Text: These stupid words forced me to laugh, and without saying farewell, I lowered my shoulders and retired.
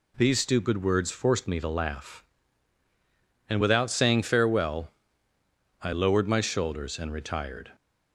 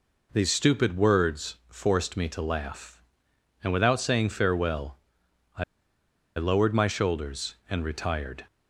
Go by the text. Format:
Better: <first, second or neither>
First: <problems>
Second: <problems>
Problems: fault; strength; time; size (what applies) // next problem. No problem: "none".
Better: first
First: none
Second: pauses between "I" and "lowered"; noticeable; at 5.6 s; 0.74 s long